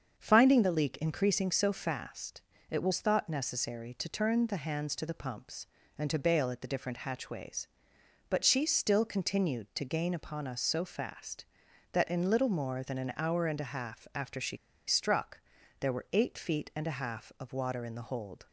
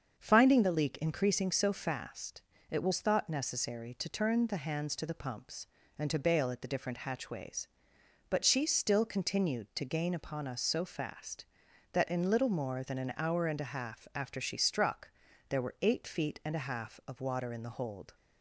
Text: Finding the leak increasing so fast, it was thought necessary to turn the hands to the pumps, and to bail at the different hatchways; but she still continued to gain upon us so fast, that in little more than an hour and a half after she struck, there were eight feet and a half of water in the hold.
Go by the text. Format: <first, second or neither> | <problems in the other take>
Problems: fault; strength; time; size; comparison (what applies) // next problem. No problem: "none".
second | starts louder than the rest; until 1.1 s; 7 dB; also in the second // pauses between "she" and "struck"; slight; at 14.5 s; 0.30 s long